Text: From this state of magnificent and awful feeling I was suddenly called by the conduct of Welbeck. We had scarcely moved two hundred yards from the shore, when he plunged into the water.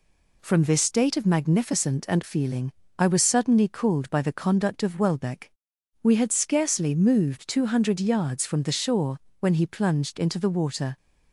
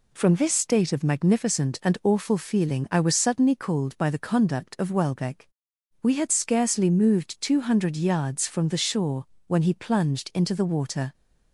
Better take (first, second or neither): second